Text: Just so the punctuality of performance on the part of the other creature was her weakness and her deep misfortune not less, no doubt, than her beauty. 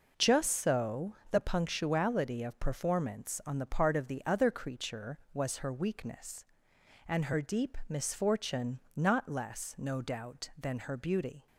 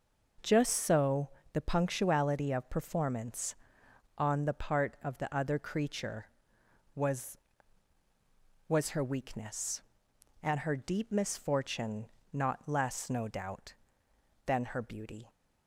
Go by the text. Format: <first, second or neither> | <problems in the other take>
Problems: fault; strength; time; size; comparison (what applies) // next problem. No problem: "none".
first | pauses between "so" and "the"; slight; at 1.2 s; 0.22 s long; slight in the first // says "was" twice; at 8.6 s // pauses between "misfortune" and "not"; slight; at 12.0 s; 0.26 s long; slight in the first